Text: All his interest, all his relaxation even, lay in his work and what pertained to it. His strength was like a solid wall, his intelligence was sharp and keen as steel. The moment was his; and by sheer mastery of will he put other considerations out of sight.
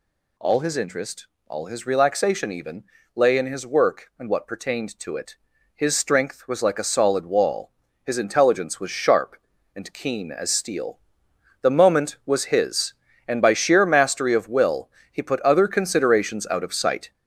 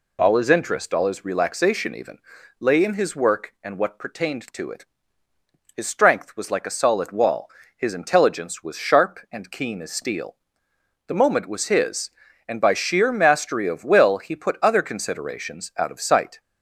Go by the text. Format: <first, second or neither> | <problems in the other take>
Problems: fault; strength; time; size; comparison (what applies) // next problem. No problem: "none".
second | gets louder; throughout; 6.5 dB // pauses between "will" and "he"; slight; at 14.8 s; 0.24 s long